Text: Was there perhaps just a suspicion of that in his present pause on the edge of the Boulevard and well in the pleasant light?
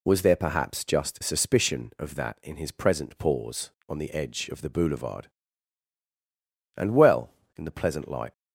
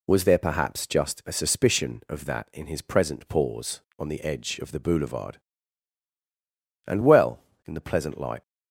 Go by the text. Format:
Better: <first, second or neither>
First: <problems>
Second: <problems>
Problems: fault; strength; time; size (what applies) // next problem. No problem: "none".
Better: second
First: skips "a"; at 1.2 s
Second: none